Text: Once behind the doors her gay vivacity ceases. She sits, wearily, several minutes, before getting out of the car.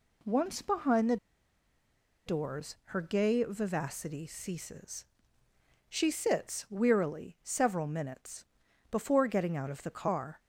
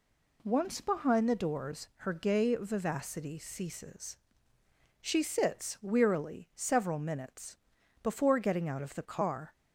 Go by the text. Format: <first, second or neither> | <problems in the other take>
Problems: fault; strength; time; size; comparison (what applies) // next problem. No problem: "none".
second | pauses between "the" and "doors"; at 1.1 s; 1.1 s long